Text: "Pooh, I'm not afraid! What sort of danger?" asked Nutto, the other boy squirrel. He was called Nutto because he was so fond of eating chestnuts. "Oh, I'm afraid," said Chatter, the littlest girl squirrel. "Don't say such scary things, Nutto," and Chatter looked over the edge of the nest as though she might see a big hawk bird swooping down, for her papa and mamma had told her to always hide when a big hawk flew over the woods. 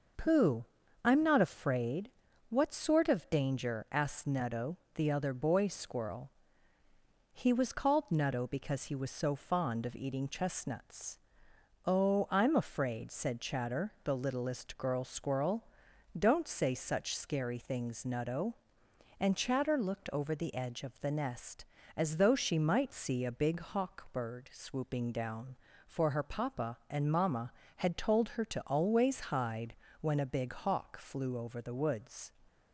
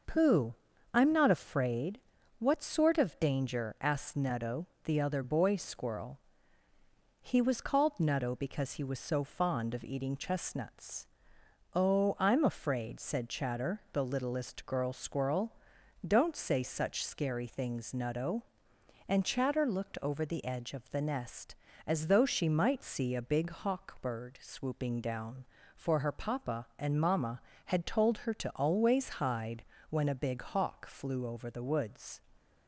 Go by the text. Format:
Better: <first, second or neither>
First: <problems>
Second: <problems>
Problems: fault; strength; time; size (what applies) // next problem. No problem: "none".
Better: neither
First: starts louder than the rest; noticeable; until 1.5 s; 6 dB // pauses between "hide" and "when"; slight; at 29.7 s; 0.26 s long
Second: starts louder than the rest; noticeable; until 1.4 s; 6 dB // pauses between "hide" and "when"; slight; at 29.6 s; 0.26 s long